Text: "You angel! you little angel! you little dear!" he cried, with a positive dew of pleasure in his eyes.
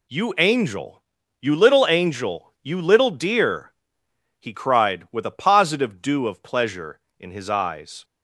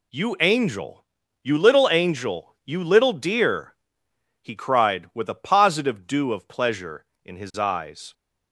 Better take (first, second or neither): neither